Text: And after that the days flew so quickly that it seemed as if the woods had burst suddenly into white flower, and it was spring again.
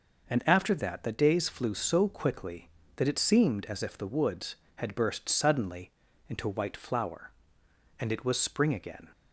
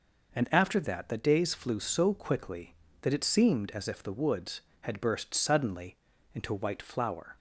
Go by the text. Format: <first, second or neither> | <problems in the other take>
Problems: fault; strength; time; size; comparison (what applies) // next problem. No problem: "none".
first | pauses between "suddenly" and "into"; at 5.9 s; 0.38 s long; also in the first // stops before "and it was spring again"; at 7.3 s